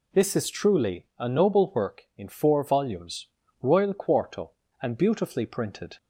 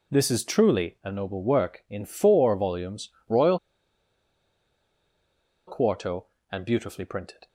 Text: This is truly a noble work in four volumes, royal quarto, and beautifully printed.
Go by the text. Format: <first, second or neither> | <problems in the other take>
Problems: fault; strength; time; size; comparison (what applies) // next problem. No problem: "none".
first | pauses between "royal" and "quarto"; strong; at 3.5 s; 2.0 s long